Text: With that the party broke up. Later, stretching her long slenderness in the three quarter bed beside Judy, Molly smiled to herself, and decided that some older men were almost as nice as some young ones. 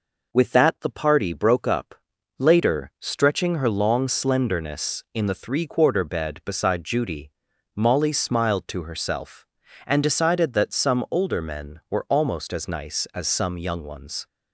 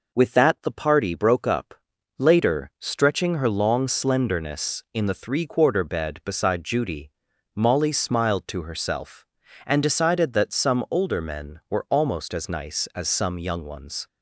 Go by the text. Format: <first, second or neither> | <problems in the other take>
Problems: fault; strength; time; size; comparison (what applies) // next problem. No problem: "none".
neither | none